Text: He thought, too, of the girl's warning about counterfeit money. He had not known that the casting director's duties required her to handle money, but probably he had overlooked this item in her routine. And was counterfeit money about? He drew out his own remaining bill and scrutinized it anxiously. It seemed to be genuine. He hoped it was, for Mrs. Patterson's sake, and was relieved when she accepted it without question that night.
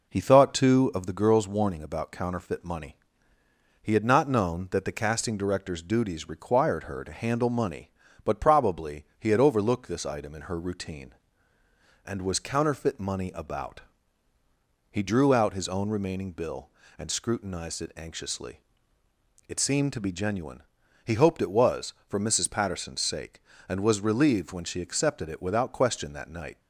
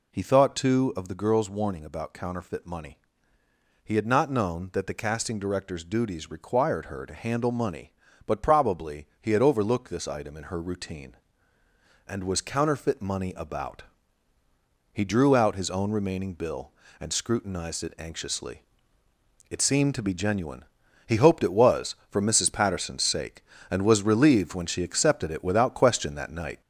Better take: first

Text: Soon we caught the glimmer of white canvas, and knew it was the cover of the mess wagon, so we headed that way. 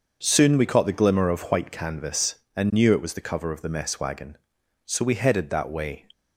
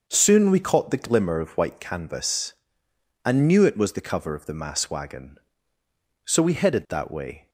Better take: first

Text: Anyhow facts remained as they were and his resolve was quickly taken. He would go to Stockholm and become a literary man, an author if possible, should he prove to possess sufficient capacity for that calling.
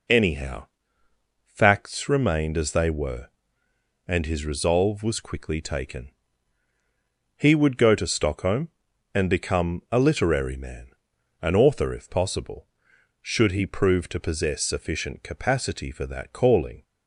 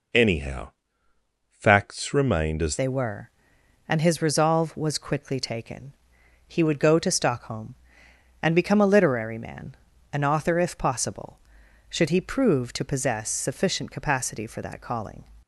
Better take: first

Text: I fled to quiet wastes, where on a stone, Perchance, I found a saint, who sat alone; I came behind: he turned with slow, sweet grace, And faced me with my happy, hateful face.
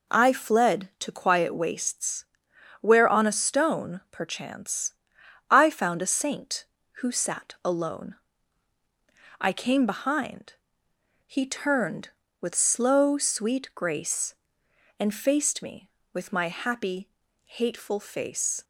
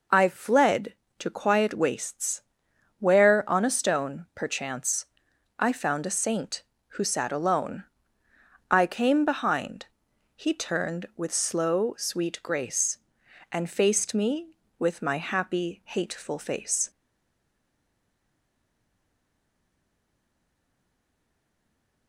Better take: first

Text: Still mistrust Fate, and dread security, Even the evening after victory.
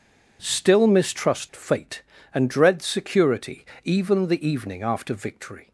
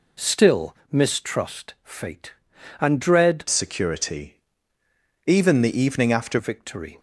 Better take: first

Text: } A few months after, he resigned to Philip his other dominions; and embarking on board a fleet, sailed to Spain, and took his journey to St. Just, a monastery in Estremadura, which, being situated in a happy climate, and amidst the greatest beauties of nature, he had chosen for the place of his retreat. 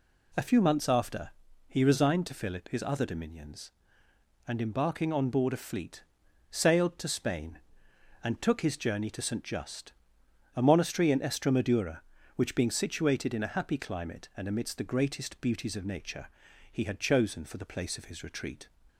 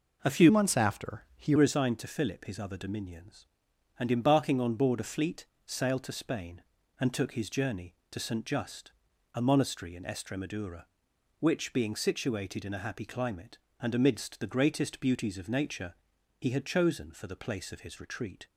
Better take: first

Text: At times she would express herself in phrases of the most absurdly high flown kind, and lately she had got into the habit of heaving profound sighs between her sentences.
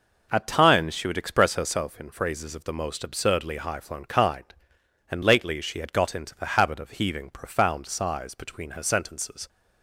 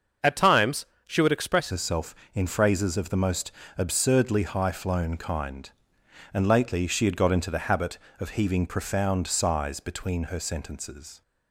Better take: first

